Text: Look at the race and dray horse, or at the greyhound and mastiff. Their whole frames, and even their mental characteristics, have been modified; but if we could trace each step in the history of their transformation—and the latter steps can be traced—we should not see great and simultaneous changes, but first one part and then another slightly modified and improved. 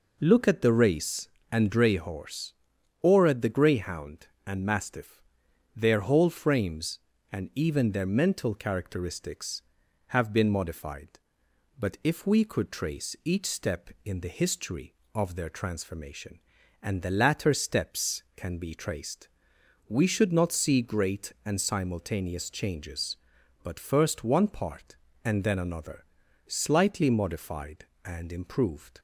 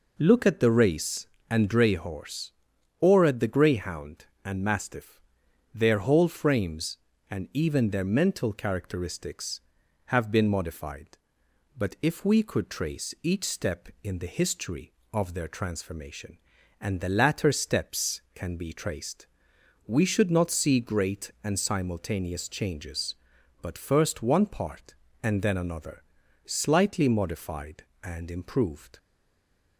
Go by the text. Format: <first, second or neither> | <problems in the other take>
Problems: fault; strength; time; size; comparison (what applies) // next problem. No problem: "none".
first | pauses between "another" and "slightly"; at 26.0 s; 0.42 s long; also in the first // stays silent after the last word; slight; from 28.9 s on; 0.8 s long